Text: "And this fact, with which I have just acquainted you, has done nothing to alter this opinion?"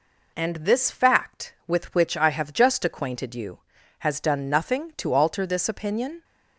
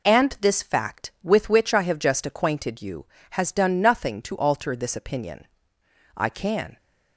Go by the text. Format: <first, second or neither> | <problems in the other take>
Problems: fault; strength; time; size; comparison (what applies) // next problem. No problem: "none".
first | goes on to say "I can"; from 6.1 s on; 0.60 s long